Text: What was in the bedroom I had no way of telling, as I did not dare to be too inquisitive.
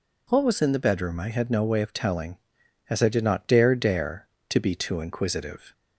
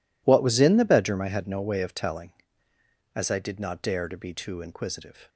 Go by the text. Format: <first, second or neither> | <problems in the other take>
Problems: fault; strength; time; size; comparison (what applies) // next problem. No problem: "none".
second | says "dare" twice; at 3.7 s